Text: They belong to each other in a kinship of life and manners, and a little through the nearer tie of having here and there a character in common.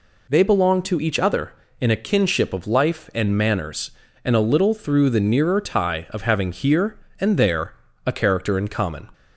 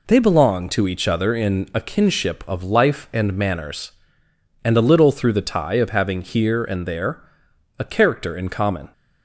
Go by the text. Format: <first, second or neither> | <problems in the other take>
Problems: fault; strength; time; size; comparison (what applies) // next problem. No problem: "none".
first | skips "nearer"; at 5.4 s // pauses between "there" and "a"; noticeable; at 7.2 s; 0.56 s long; slight in the first